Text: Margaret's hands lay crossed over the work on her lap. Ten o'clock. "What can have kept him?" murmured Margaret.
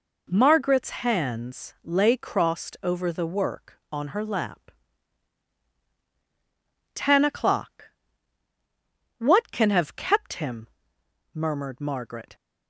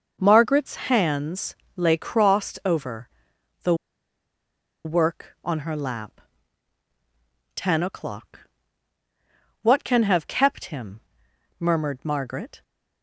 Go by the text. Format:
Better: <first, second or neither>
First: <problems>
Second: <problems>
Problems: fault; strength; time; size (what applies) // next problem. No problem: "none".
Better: first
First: none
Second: starts louder than the rest; until 1.2 s; 6 dB // pauses between "hands" and "lay"; slight; at 1.5 s; 0.18 s long // pauses between "over" and "the"; noticeable; at 3.0 s; 0.56 s long // pauses between "the" and "work"; at 3.7 s; 1.1 s long